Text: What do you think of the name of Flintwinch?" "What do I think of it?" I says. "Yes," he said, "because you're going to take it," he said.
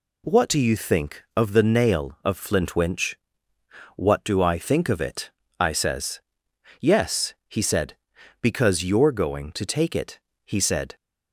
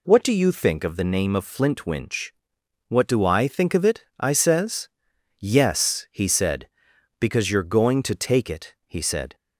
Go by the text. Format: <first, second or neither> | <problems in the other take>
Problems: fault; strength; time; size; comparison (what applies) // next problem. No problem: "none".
second | says "nail" for "name"; at 1.9 s